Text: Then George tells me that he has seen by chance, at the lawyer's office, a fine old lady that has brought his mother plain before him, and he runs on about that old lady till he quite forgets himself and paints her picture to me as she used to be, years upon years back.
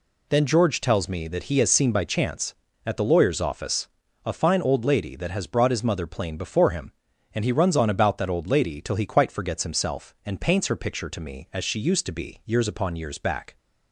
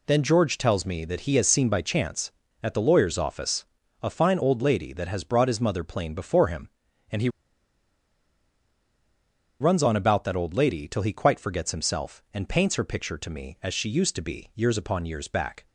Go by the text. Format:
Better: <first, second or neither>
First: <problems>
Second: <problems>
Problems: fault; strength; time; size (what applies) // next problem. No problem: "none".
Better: first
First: none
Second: pauses between "he" and "runs"; strong; at 7.2 s; 2.3 s long